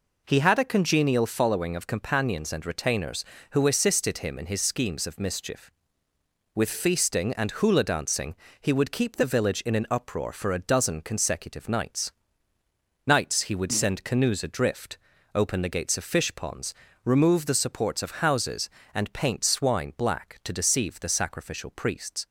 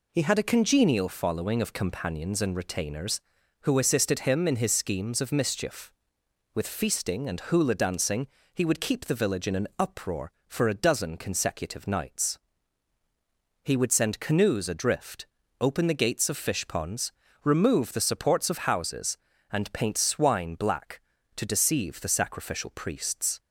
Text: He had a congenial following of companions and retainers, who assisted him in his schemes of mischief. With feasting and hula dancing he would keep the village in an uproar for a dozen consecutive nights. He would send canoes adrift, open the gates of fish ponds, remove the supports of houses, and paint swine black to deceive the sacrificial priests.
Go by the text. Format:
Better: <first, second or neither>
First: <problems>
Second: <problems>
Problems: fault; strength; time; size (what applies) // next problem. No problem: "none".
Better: second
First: pauses between "dancing" and "he"; slight; at 8.3 s; 0.28 s long // says "nights" twice; at 13.0 s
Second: pauses between "dancing" and "he"; slight; at 8.2 s; 0.26 s long